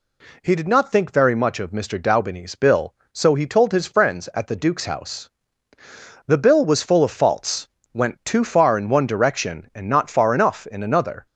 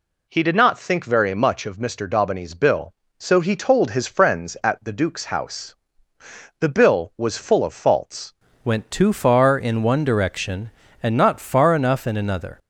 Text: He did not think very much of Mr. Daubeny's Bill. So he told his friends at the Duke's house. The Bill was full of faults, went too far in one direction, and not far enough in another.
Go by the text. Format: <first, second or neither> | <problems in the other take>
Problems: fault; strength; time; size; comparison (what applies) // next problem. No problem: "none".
first | changes voice at "went"; from 8.6 s on; 3.9 s long